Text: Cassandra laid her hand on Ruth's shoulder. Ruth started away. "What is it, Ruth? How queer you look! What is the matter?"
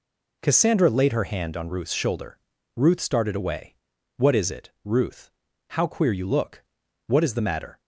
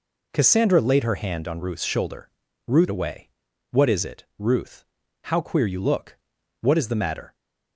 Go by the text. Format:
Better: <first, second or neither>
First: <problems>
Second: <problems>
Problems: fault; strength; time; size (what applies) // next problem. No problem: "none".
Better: first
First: none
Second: skips "started"; at 2.8 s